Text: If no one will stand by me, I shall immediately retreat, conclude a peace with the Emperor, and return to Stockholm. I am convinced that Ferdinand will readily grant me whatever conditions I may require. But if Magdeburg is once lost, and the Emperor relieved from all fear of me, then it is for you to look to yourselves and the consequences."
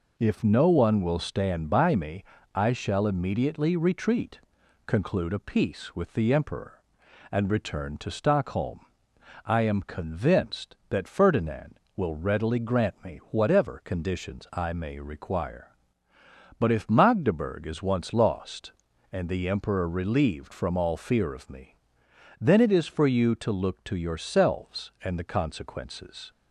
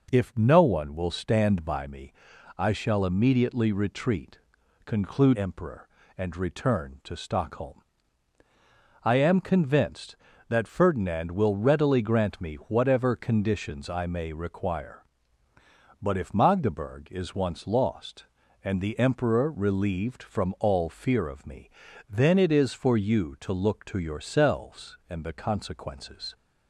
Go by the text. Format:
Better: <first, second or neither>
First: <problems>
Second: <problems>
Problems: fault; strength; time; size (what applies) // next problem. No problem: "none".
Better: first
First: none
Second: skips "a peace with the"; at 5.3 s